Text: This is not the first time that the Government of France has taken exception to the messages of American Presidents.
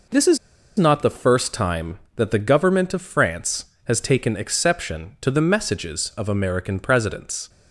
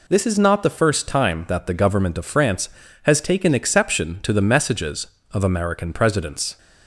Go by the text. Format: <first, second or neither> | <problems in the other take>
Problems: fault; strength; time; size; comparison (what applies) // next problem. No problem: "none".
second | pauses between "is" and "not"; at 0.3 s; 0.40 s long